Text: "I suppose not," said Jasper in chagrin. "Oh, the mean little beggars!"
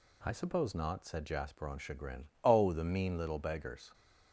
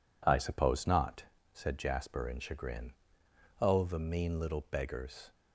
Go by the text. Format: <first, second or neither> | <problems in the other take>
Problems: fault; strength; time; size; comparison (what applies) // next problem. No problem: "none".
second | says "on" for "in"; at 1.6 s